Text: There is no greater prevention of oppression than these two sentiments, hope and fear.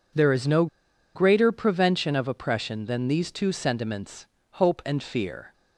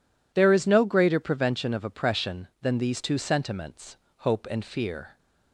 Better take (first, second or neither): second